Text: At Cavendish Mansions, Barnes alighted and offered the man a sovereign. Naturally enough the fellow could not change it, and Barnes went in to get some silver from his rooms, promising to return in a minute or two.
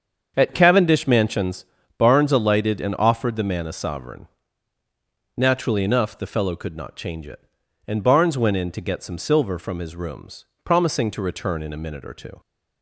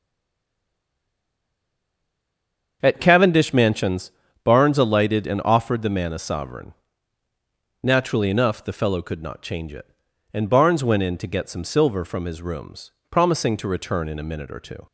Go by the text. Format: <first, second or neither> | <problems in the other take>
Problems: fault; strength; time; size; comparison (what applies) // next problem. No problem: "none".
first | stays silent before the first word; strong; until 2.8 s; 2.8 s long // starts louder than the rest; until 3.8 s; 7 dB; also in the first